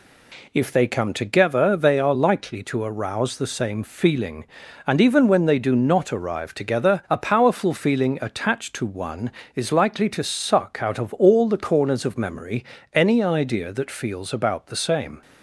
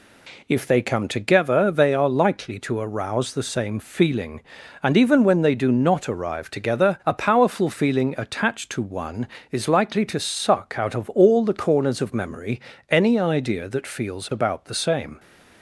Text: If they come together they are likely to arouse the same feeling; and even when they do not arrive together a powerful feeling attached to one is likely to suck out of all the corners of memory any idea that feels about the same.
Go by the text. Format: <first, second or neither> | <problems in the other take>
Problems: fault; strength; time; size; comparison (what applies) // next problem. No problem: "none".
neither | pauses between "memory" and "any"; slight; the same in both